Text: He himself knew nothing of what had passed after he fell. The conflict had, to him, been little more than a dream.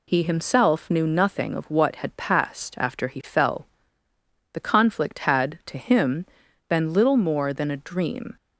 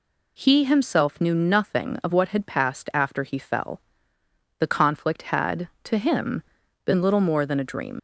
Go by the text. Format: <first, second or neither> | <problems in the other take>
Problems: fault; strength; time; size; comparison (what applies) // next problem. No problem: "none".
first | leaves "dream" unfinished; at 7.9 s; 90 ms